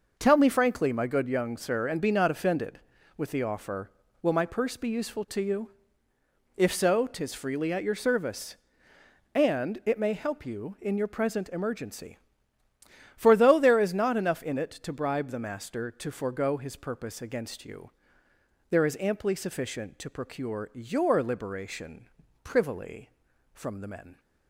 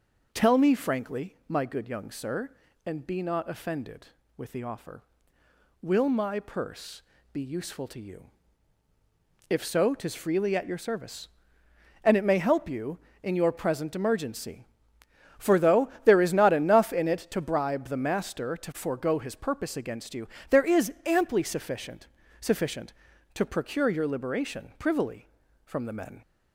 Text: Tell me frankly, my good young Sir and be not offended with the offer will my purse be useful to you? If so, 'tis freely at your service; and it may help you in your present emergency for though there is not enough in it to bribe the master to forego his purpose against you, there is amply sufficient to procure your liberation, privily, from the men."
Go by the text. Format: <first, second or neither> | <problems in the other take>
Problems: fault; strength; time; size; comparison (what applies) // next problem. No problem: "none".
first | pauses between "purse" and "be"; slight; at 7.0 s; 0.30 s long // says "sufficient" twice; at 22.3 s